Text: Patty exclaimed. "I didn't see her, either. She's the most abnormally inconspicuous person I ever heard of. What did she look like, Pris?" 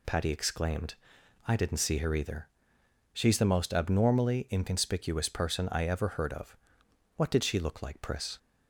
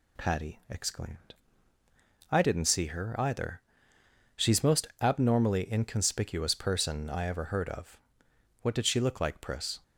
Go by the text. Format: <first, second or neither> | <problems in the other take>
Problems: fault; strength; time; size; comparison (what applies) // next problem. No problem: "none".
first | skips "the"; at 4.6 s